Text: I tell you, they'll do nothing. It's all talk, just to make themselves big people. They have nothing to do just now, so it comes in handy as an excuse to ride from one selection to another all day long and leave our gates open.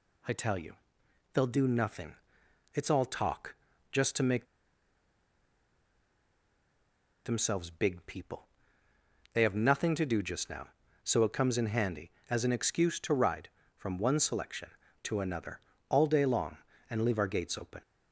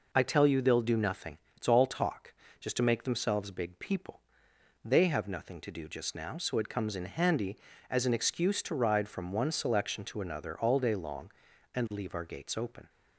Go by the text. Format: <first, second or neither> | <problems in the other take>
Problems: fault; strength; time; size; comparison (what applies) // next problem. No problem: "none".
second | pauses between "make" and "themselves"; strong; at 4.4 s; 2.7 s long // pauses between "another" and "all"; slight; at 15.5 s; 0.30 s long